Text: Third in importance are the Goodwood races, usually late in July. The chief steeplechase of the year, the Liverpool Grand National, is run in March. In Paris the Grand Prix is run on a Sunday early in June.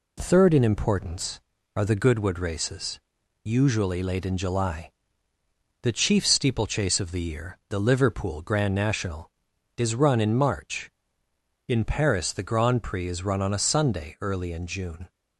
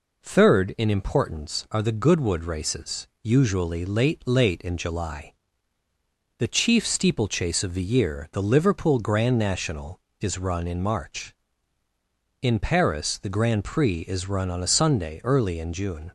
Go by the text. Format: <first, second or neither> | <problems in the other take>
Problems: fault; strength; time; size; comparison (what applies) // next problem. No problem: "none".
first | says "late" twice; at 4.2 s